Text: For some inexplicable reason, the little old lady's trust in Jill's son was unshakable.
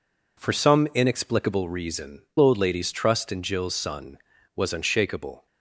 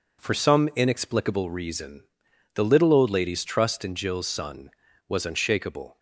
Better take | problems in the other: second | skips "the little"; at 2.3 s

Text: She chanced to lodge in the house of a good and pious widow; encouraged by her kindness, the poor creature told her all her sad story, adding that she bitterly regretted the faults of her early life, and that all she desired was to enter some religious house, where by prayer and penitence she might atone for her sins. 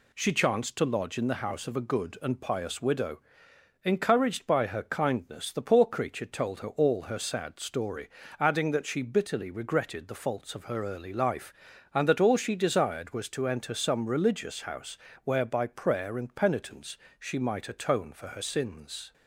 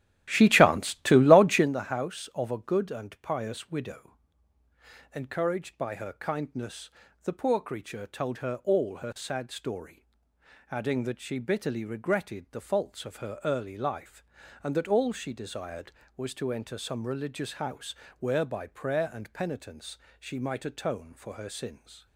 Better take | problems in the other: first | starts louder than the rest; strong; until 1.7 s; 13 dB // pauses between "penitence" and "she"; slight; at 19.9 s; 0.20 s long; slight in the first

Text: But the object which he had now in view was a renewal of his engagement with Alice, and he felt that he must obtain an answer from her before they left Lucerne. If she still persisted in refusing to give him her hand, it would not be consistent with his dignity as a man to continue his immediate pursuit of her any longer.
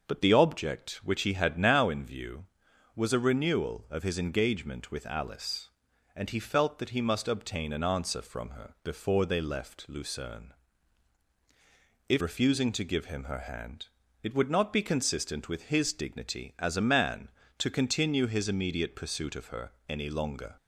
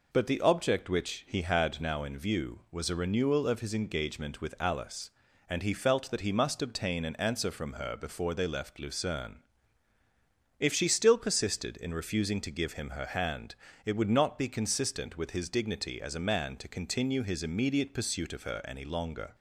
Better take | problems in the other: second | starts louder than the rest; until 1.1 s; 6 dB // skips "she still persisted in"; at 12.2 s // pauses between "her" and "any"; slight; at 19.7 s; 0.16 s long

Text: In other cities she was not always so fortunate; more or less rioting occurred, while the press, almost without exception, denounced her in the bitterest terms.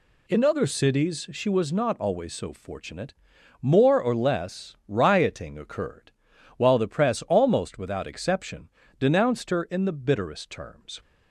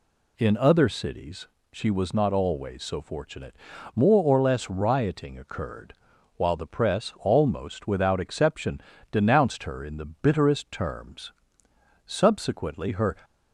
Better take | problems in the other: first | pauses between "cities" and "she"; slight; at 1.4 s; 0.24 s long // pauses between "the" and "bitterest"; slight; at 10.0 s; 0.20 s long // goes on to say "Subsequently her"; noticeable; from 12.0 s on; 1.1 s long

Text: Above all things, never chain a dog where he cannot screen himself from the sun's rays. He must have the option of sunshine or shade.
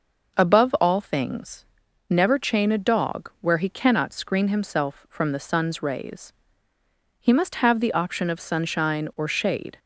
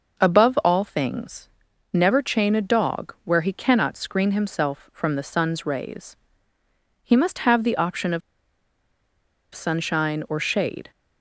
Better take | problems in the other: first | pauses between "of" and "sunshine"; strong; at 8.2 s; 1.3 s long

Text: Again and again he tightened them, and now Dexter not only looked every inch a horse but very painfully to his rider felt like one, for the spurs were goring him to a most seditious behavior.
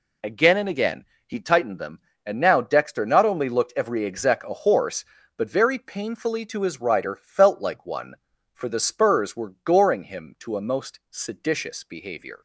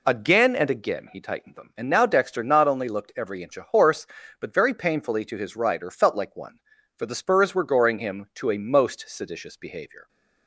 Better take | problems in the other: second | pauses between "again" and "he"; slight; at 1.0 s; 0.22 s long // says "exec" for "inch"; at 4.0 s

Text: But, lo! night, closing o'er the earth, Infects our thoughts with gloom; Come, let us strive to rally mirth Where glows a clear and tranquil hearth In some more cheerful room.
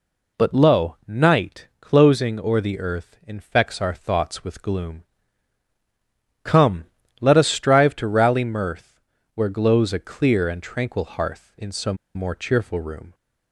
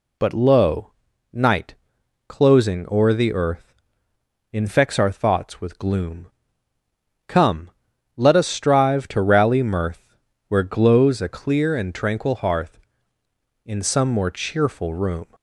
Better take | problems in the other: second | pauses between "mirth" and "Where"; slight; at 9.0 s; 0.34 s long; slight in the second // pauses between "some" and "more"; slight; at 11.9 s; 0.18 s long

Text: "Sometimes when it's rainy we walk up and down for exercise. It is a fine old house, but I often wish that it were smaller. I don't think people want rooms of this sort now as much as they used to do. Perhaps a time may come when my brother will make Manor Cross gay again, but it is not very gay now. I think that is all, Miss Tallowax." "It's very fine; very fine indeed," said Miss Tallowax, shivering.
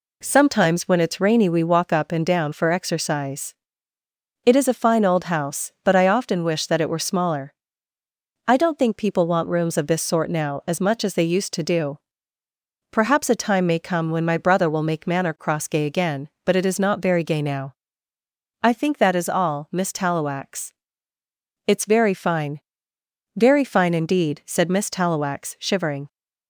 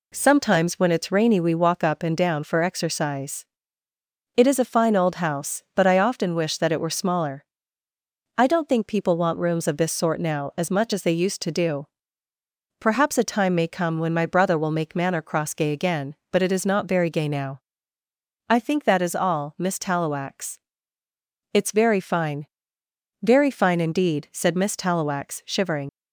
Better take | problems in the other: first | leaves "shivering" unfinished; at 25.8 s; 50 ms

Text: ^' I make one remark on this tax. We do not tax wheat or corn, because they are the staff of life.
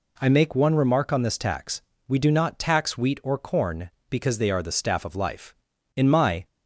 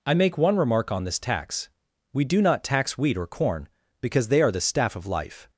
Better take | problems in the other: second | goes on to say "In my"; from 5.9 s on; 0.52 s long

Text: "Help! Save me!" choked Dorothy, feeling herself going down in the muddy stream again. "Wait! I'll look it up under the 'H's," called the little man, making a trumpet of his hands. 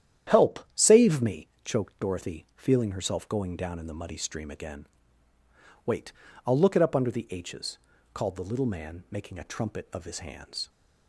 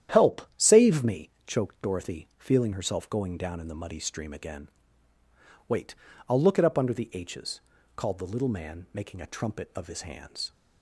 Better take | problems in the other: neither | starts louder than the rest; strong; the same in both

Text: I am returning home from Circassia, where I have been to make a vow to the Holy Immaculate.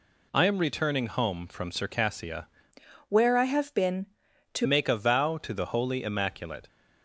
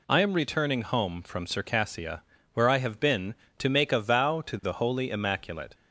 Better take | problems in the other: second | changes voice from "where" to "to"; from 3.0 to 4.6 s; 1.6 s long

